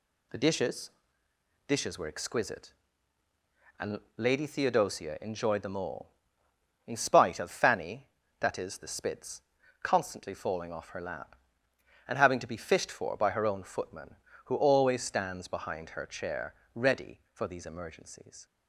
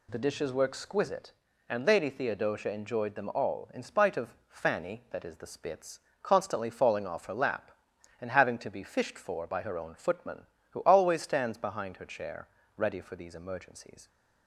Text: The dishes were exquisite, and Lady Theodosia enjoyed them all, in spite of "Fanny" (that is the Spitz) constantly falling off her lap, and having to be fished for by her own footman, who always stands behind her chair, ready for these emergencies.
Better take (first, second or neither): second